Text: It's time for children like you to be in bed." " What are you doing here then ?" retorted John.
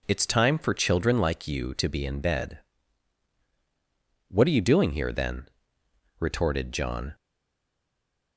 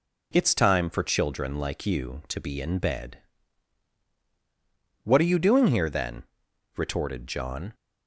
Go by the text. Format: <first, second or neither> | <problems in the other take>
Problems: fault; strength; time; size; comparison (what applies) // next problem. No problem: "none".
second | stays silent after the last word; noticeable; from 7.1 s on; 1.2 s long